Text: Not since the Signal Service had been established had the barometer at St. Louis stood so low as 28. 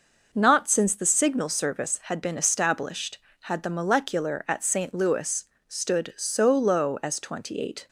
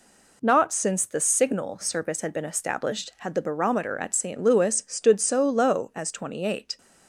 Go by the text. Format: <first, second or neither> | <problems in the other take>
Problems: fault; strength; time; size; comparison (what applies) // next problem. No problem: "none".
second | says "molecular" for "barometer"; at 3.6 s // pauses between "Louis" and "stood"; slight; at 5.4 s; 0.24 s long